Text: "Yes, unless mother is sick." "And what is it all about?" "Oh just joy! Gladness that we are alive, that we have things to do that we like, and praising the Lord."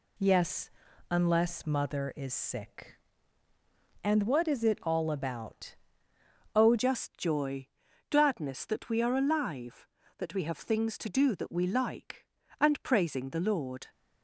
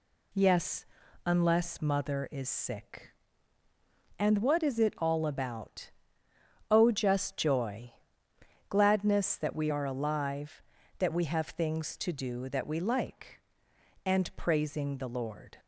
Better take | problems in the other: second | changes voice at "just"; from 6.7 s on; 7.1 s long

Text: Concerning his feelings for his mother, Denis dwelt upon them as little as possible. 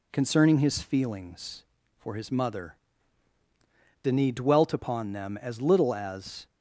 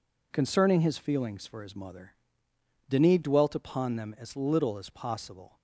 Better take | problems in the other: second | stops before "possible"; at 6.4 s

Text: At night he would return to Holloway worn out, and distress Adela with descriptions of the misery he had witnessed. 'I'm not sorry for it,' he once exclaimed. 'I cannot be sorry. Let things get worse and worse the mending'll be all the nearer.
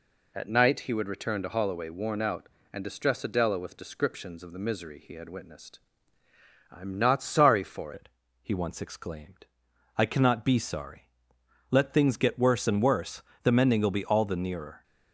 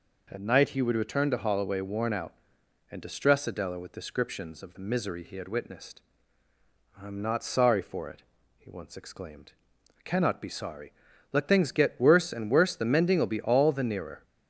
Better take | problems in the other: second | changes voice at "it"; from 7.9 s on; 6.9 s long // pauses between "worse" and "the"; slight; at 13.2 s; 0.22 s long

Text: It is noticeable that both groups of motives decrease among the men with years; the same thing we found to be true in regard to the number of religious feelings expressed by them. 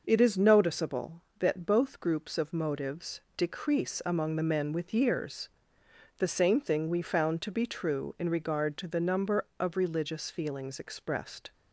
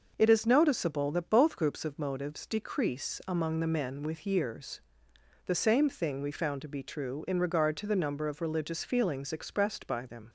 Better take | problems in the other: second | pauses between "motives" and "decrease"; slight; at 3.2 s; 0.16 s long // stops before "by them"; at 11.5 s

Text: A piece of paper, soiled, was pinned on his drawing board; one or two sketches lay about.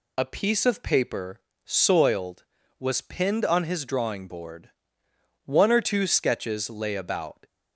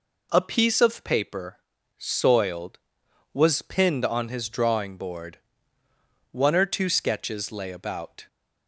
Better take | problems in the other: neither | none

